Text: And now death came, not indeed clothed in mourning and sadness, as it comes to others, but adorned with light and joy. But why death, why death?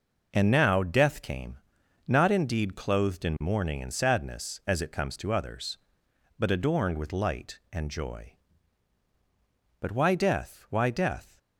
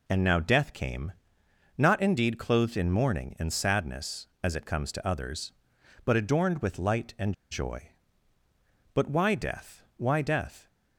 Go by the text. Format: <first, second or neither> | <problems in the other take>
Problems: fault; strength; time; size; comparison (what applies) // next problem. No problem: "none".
first | pauses between "and" and "joy"; slight; at 7.3 s; 0.19 s long